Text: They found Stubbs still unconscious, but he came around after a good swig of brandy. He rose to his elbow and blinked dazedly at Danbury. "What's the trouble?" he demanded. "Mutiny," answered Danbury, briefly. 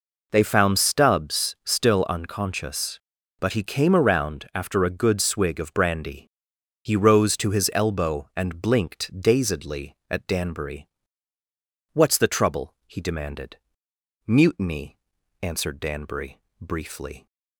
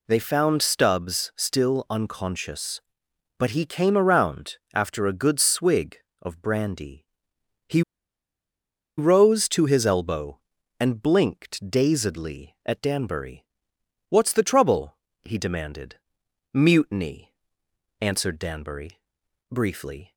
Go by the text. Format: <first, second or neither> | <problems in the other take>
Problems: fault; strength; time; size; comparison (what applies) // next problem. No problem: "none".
first | pauses between "around" and "after"; slight; at 4.5 s; 0.16 s long // pauses between "He" and "rose"; at 7.8 s; 1.1 s long